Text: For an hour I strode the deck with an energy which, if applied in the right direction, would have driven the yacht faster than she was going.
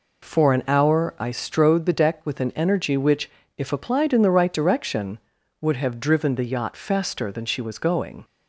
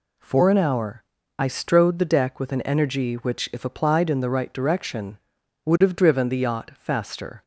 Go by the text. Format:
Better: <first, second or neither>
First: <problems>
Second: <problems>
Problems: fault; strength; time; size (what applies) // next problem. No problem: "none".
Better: first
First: none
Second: pauses between "hour" and "I"; slight; at 1.0 s; 0.34 s long // stops before "than she was going"; at 7.4 s